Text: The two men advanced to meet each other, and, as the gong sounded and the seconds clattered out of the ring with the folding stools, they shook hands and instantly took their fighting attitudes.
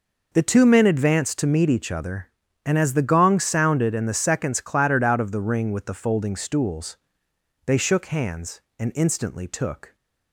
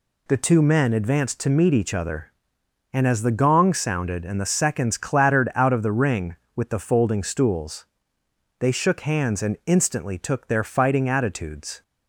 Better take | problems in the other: second | stops before "their fighting attitudes"; at 9.9 s

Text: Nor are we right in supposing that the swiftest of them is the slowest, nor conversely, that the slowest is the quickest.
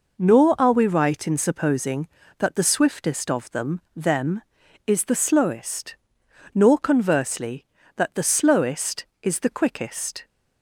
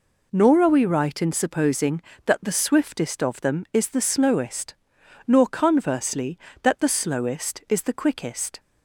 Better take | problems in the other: second | says "them" twice; at 3.9 s

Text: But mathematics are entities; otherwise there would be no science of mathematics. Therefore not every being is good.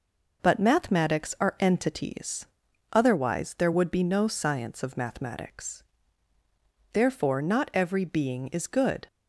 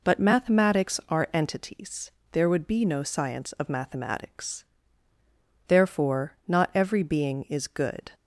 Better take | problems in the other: first | skips "otherwise"; at 2.2 s // pauses between "Therefore" and "not"; slight; at 6.3 s; 0.16 s long

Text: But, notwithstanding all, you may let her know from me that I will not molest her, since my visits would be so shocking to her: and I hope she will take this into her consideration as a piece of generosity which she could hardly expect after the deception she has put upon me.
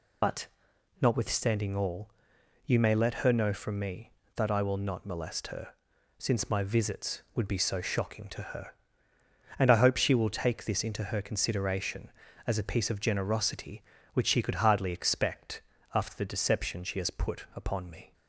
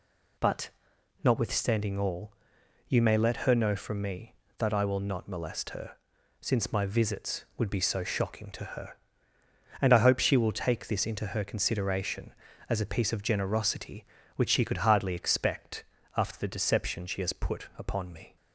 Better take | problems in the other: second | loses the start of "But"; at 0.2 s; 55 ms // pauses between "expect" and "after"; slight; at 15.6 s; 0.32 s long; slight in the second

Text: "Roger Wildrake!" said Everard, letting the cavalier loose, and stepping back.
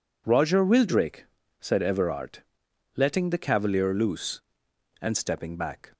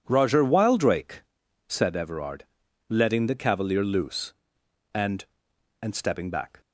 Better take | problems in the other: first | says "and" twice; at 5.8 s

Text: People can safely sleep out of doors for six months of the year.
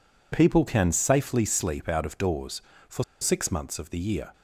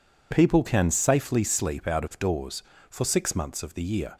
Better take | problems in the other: second | pauses between "for" and "six"; slight; at 3.0 s; 0.17 s long

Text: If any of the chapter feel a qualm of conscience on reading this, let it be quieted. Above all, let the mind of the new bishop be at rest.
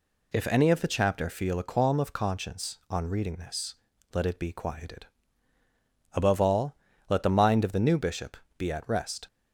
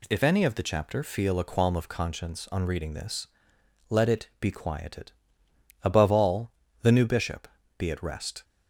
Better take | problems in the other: first | skips "let the mind of"; at 6.6 s // pauses between "bishop" and "be"; slight; at 7.4 s; 0.30 s long; slight in the first

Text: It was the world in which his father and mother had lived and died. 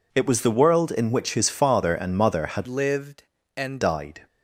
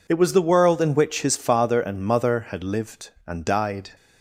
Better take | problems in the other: second | changes voice from "lived" to "and"; from 2.6 to 3.8 s; 1.2 s long

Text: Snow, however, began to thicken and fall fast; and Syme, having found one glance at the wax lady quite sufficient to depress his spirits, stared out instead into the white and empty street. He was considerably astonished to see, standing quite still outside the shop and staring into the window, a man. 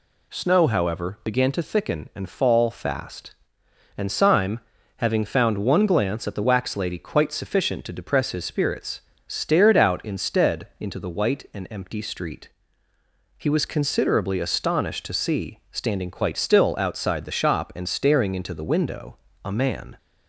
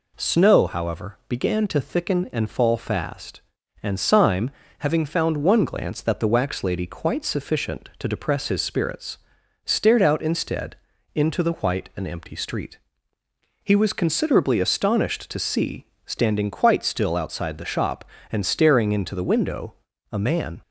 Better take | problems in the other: first | says "that" for "at"; at 5.9 s // pauses between "instead" and "into"; at 10.7 s; 0.40 s long

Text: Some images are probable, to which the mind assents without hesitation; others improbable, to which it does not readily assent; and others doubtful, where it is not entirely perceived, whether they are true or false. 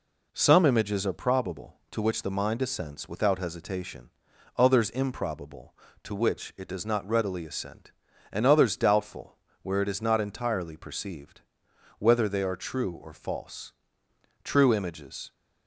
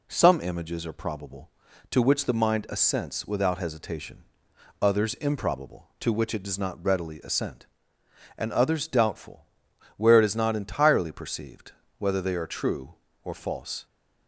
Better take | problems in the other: second | goes on to say "True images"; noticeable; from 14.4 s on; 0.88 s long

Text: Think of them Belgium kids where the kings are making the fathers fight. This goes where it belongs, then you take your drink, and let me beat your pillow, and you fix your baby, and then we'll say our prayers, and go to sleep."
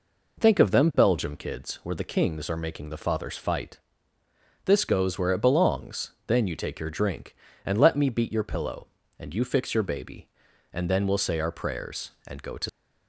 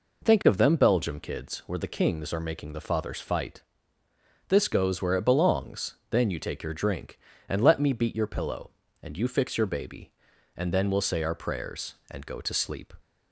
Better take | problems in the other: second | stops before "sleep"; at 12.6 s

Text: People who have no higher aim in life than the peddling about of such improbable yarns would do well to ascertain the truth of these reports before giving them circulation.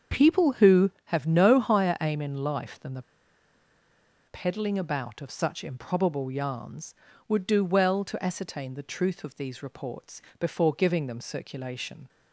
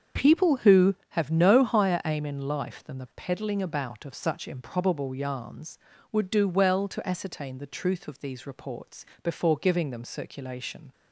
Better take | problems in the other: second | starts louder than the rest; until 1.2 s; 7 dB; also in the second // pauses between "the" and "peddling"; strong; at 3.0 s; 1.2 s long // pauses between "reports" and "before"; slight; at 10.2 s; 0.16 s long; slight in the second

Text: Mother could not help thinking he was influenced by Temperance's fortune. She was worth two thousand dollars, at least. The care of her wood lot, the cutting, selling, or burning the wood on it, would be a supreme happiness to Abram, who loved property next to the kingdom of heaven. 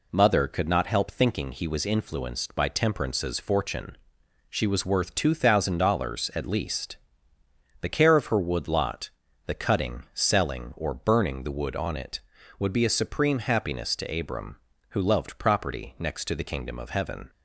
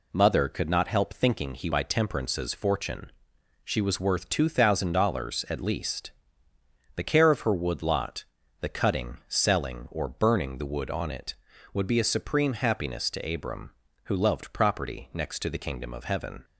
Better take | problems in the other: first | skips "was influenced"; at 1.7 s

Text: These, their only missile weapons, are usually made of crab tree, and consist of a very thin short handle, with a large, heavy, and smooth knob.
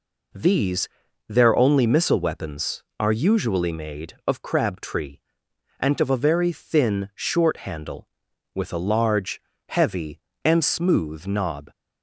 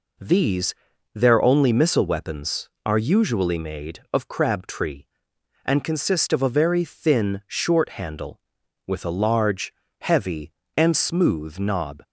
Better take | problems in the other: second | skips "consist"; at 5.9 s

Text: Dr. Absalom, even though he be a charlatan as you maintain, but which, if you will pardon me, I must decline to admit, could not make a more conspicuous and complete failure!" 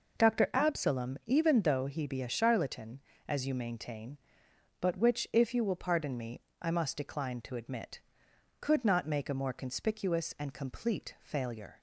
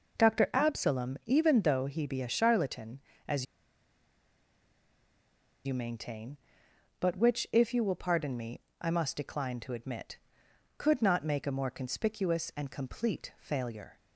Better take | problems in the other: first | pauses between "as" and "you"; strong; at 3.4 s; 2.2 s long

